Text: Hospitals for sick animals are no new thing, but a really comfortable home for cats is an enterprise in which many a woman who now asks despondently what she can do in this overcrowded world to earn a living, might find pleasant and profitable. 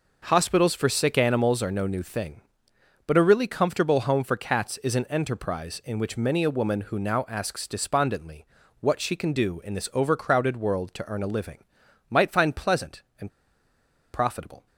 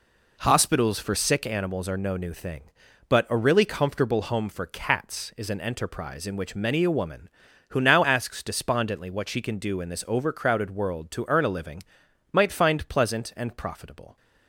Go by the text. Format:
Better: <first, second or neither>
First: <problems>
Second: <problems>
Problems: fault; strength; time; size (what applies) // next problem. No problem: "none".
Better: second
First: pauses between "despondently" and "what"; slight; at 8.4 s; 0.34 s long // pauses between "and" and "profitable"; noticeable; at 13.2 s; 0.84 s long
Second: none